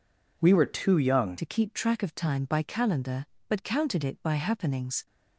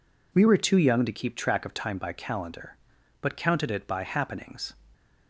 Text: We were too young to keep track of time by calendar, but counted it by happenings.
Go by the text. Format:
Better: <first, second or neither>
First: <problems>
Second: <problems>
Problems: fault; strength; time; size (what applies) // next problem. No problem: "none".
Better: second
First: changes voice at "to"; from 1.3 s on; 3.7 s long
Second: none